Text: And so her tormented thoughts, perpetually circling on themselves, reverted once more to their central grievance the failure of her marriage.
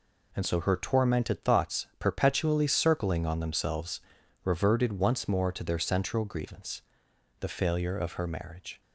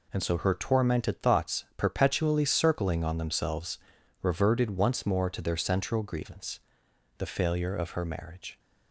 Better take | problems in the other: neither | pauses between "grievance" and "the"; noticeable; the same in both

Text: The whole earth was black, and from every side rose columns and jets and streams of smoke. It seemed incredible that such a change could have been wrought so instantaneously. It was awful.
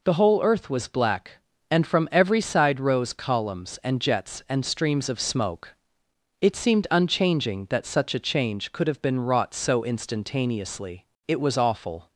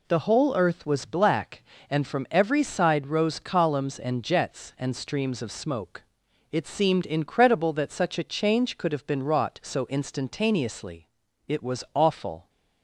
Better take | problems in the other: second | says "unchanging" for "incredible"; at 6.9 s

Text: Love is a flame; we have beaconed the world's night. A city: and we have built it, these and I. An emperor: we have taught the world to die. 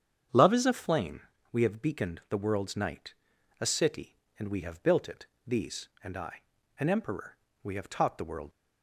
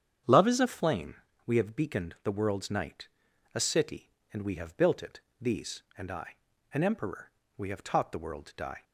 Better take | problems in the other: second | starts louder than the rest; strong; until 1.6 s; 8 dB; strong in the second // stops before "to die"; at 8.5 s

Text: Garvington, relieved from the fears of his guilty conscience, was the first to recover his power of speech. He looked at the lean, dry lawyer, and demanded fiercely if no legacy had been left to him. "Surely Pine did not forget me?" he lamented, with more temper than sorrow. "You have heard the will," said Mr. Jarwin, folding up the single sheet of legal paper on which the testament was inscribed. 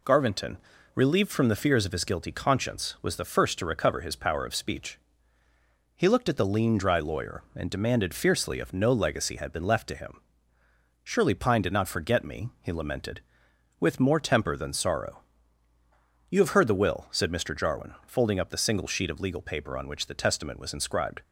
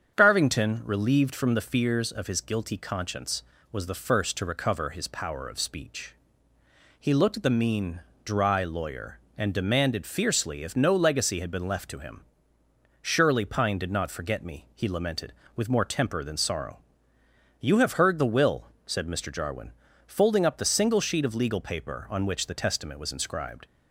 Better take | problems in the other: first | starts louder than the rest; strong; until 1.1 s; 7.5 dB // says "mean" for "lean"; at 7.4 s

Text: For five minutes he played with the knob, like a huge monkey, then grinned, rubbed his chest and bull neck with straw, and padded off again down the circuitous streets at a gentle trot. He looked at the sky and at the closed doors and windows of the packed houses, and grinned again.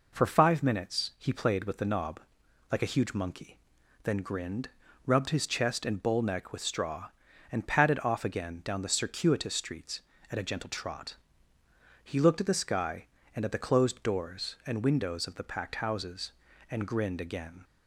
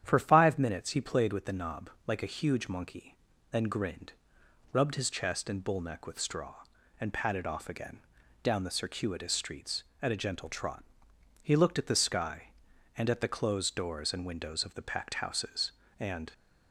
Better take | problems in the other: first | starts louder than the rest; strong; until 1.0 s; 9.5 dB // pauses between "again" and "down"; at 8.0 s; 0.42 s long // stops before "grinned again"; at 16.3 s

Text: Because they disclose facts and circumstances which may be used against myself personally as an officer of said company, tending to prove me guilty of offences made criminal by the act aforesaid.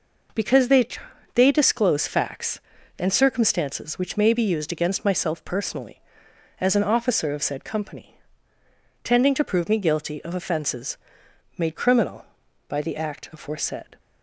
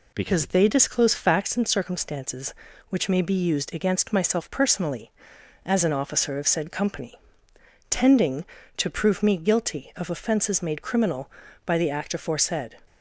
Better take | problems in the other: second | says "they" twice; at 1.3 s // pauses between "offences" and "made"; noticeable; at 10.9 s; 0.60 s long

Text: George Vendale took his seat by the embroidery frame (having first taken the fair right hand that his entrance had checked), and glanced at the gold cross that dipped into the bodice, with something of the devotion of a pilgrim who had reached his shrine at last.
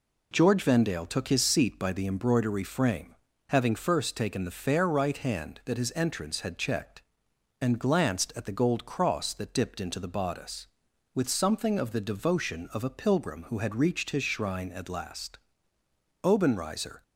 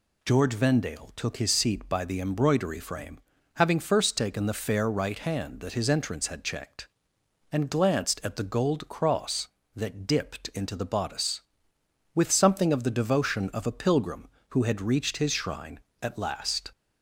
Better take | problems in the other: second | goes on to say "Obenreizer"; noticeable; from 16.2 s on; 0.78 s long

